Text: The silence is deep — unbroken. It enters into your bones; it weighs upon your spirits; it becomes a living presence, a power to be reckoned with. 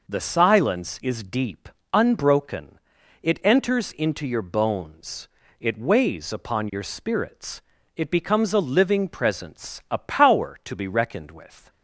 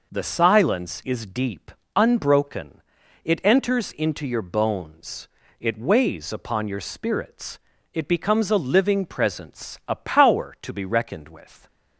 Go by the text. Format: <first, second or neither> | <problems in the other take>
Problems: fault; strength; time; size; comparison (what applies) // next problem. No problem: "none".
neither | none